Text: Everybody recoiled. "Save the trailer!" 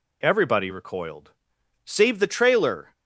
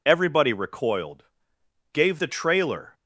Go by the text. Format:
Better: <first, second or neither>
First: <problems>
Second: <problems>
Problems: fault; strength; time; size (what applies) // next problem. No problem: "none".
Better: first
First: none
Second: says "Gave" for "Save"; at 1.9 s